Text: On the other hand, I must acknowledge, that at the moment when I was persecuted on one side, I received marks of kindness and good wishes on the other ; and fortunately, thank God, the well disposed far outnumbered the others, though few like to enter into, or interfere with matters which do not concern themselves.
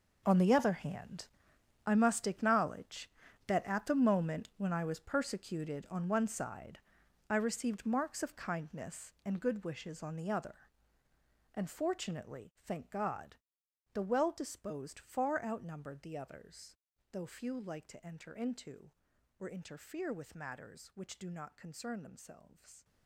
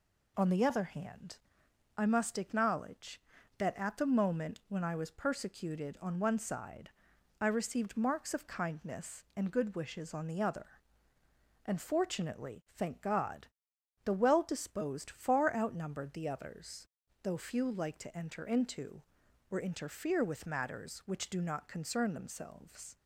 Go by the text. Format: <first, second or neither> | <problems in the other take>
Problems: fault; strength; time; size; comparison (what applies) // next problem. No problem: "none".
second | gets quieter; strong; throughout; 15 dB